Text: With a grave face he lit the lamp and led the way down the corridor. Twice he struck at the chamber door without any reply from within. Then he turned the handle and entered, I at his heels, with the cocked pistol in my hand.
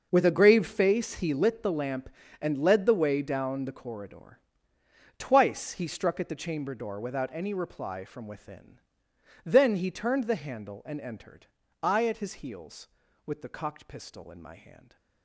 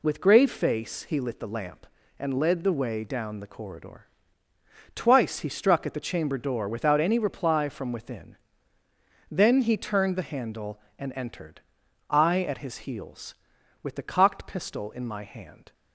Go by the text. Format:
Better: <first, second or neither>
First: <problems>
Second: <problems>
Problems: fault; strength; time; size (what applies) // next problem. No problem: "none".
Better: first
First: none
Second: skips "a"; at 0.2 s